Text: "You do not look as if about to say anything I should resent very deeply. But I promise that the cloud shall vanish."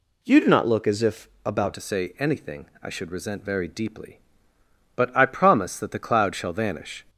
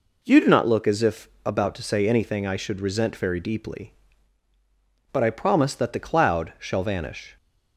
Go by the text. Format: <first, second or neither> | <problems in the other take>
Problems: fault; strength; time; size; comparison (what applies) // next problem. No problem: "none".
second | pauses between "if" and "about"; slight; at 1.2 s; 0.16 s long; slight in the second // changes voice at "to"; from 1.7 s on; 5.3 s long // pauses between "anything" and "I"; slight; at 2.6 s; 0.16 s long